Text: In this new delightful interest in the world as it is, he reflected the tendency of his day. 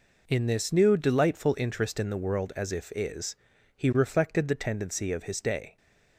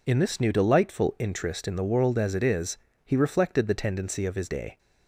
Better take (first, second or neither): second